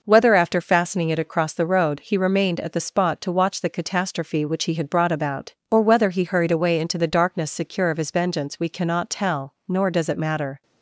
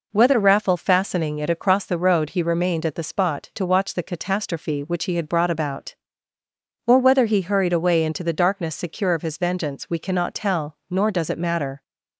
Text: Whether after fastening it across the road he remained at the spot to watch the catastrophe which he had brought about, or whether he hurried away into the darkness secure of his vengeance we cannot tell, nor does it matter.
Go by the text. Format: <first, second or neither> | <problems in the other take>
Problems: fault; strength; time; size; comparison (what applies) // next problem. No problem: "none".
first | says "raffle" for "after"; at 0.4 s